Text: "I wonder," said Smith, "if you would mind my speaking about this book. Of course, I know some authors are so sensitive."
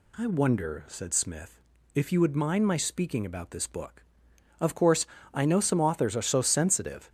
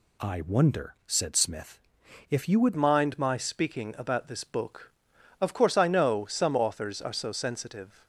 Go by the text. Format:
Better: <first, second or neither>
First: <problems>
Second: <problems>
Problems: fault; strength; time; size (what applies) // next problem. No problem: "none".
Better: first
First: none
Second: changes voice at "mind"; from 2.7 s on; 5.3 s long